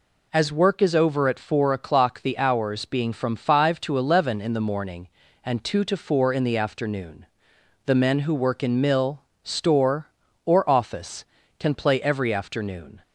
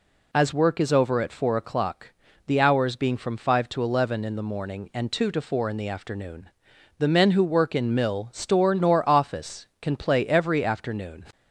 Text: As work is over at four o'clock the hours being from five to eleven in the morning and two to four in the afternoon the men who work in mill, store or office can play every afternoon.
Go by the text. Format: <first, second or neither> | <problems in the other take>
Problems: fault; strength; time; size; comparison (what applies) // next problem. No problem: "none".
first | pauses between "o'clock" and "the"; slight; at 2.1 s; 0.32 s long // pauses between "afternoon" and "the"; noticeable; at 6.4 s; 0.50 s long; noticeable in the first // says "nor" for "or"; at 8.7 s